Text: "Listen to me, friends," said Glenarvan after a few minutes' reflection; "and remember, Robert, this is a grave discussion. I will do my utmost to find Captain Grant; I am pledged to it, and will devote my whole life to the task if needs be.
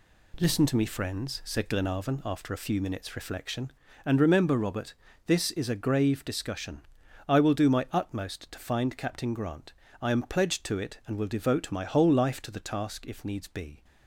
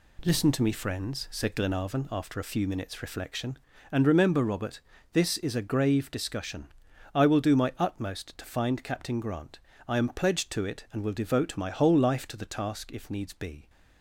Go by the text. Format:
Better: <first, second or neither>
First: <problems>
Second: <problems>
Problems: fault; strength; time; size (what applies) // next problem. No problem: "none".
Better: neither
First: none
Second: none